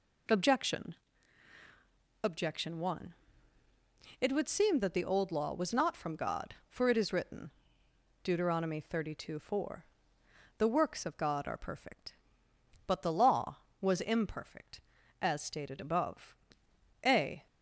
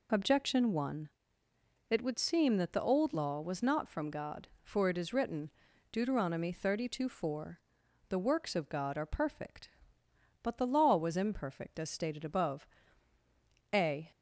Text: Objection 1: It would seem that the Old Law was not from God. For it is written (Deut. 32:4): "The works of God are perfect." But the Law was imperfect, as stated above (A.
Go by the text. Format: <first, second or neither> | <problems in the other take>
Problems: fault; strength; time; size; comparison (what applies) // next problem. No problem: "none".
second | says "Objection" twice; at 2.2 s